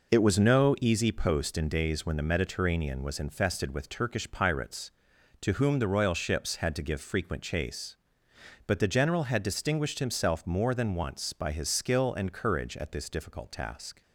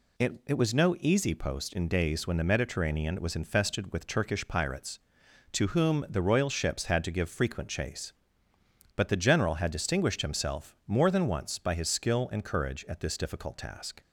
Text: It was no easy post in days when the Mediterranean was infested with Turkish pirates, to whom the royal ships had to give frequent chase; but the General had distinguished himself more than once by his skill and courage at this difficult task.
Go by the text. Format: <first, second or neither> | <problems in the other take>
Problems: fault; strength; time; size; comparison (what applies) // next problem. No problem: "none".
first | says "It" twice; at 0.4 s